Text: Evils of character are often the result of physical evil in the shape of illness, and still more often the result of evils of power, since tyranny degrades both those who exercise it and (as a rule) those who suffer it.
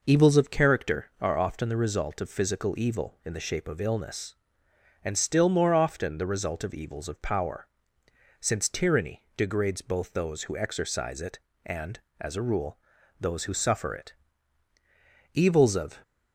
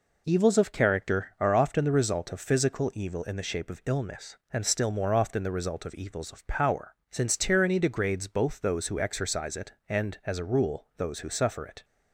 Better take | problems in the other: second | goes on to say "Evils of"; noticeable; from 15.3 s on; 0.68 s long

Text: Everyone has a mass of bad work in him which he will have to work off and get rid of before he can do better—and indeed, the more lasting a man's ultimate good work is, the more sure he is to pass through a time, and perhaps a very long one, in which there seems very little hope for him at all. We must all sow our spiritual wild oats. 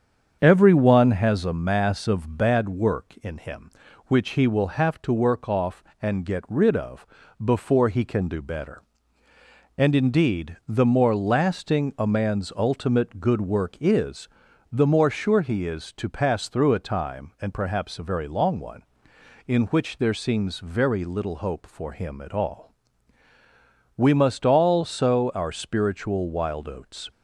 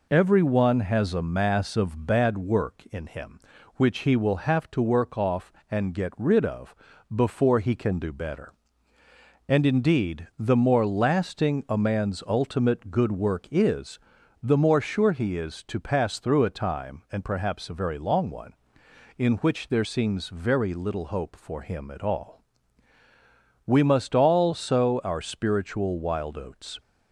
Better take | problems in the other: second | starts louder than the rest; strong; until 1.3 s; 7.5 dB // pauses between "of" and "before"; at 7.0 s; 0.38 s long; also in the second

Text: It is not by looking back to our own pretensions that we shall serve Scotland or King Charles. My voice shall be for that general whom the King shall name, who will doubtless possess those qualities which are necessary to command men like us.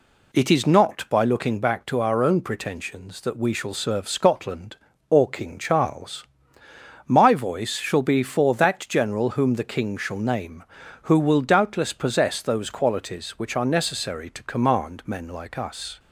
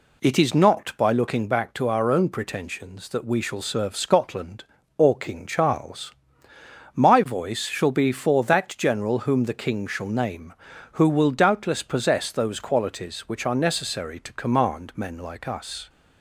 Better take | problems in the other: neither | none

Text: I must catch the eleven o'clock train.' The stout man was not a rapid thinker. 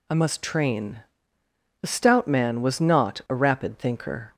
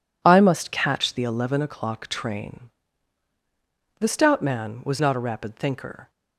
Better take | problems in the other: second | skips "catch the eleven o'clock"; at 0.4 s

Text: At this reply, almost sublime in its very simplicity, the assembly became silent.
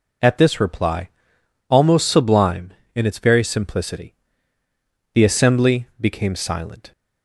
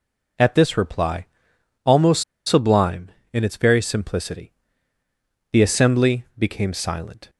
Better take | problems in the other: first | pauses between "almost" and "sublime"; slight; at 2.2 s; 0.23 s long

